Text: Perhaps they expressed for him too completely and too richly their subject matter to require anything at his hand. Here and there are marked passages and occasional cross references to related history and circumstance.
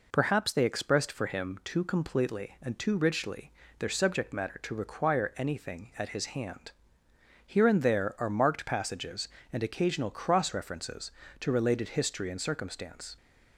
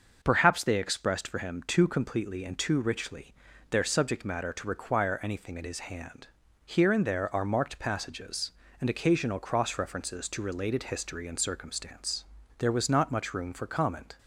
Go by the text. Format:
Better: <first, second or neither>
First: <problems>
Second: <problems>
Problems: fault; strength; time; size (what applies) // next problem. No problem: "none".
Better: first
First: pauses between "richly" and "their"; slight; at 3.5 s; 0.26 s long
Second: starts louder than the rest; until 1.2 s; 6 dB // pauses between "richly" and "their"; at 3.3 s; 0.38 s long // goes on to say "There was not much room for comment"; from 12.5 s on; 1.6 s long